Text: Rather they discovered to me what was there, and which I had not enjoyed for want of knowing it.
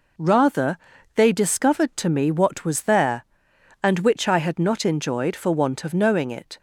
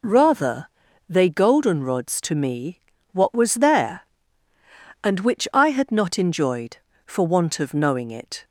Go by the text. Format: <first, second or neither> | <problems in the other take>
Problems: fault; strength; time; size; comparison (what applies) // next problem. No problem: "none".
first | pauses between "Rather" and "they"; at 0.6 s; 0.40 s long; also in the first // says "goldenrods" for "discovered"; at 1.3 s // pauses between "me" and "what"; slight; at 2.8 s; 0.30 s long